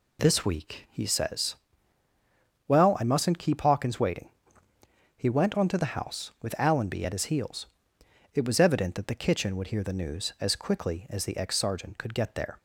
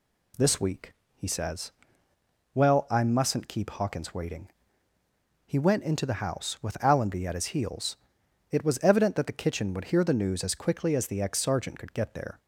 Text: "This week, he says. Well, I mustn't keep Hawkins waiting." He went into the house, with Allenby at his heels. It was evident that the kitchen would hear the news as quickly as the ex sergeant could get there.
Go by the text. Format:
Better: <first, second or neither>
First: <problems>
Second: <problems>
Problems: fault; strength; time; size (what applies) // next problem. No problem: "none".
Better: second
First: says "onto" for "into"; at 5.5 s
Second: none